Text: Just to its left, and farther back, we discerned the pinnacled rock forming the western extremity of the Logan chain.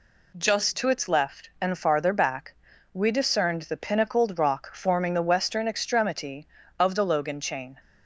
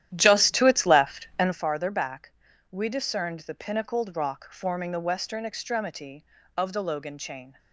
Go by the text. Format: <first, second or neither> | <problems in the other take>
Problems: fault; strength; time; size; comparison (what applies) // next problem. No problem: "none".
first | starts louder than the rest; strong; until 1.6 s; 11.5 dB